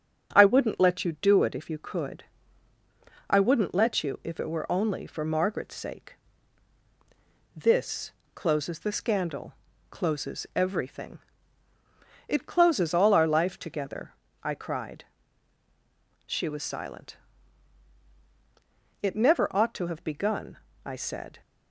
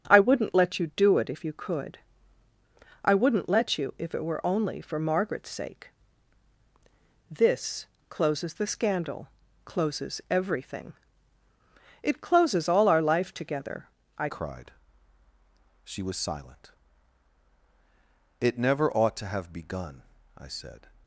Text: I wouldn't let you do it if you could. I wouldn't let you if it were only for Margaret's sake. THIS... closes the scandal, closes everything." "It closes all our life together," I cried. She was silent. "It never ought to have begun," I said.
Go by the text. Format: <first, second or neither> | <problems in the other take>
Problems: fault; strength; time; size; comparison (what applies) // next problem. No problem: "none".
first | starts louder than the rest; strong; until 1.1 s; 7.5 dB; strong in the first // changes voice at "cried"; from 14.2 s on; 6.6 s long